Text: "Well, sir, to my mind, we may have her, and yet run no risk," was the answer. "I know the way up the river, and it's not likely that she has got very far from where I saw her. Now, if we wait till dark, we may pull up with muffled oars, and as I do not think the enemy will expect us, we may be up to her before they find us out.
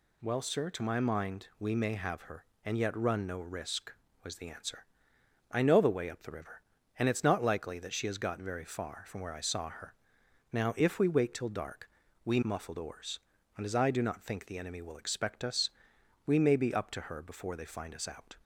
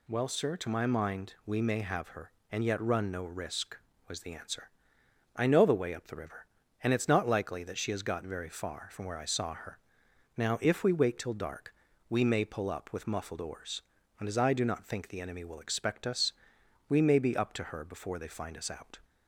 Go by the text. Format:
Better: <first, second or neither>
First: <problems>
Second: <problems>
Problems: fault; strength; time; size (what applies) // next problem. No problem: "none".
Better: second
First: skips "may pull up with"; at 12.4 s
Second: none